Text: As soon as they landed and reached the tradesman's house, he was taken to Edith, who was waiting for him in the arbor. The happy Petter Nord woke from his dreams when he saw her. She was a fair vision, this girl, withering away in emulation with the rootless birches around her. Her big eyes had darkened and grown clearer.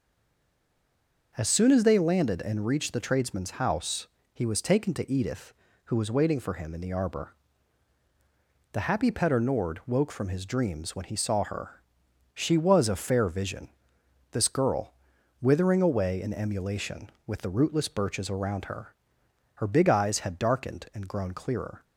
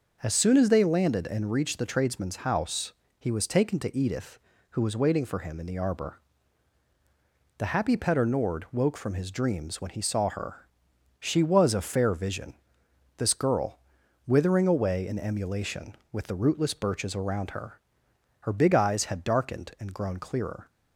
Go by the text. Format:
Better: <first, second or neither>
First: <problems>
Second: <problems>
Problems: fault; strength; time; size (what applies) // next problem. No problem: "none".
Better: second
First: stays silent before the first word; noticeable; until 1.3 s; 1.3 s long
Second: none